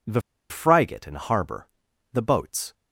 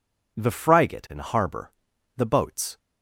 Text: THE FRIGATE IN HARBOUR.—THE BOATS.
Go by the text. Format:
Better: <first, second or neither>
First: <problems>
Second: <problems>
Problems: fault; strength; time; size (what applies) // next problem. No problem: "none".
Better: second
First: pauses between "THE" and "FRIGATE"; slight; at 0.2 s; 0.29 s long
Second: none